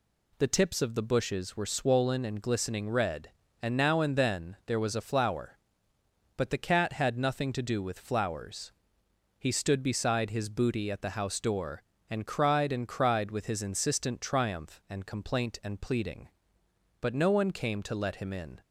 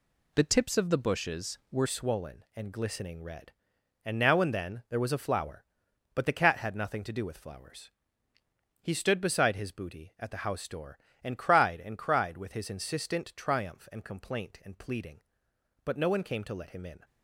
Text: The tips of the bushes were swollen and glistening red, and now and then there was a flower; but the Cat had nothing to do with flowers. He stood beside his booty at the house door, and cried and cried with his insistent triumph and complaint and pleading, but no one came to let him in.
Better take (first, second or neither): first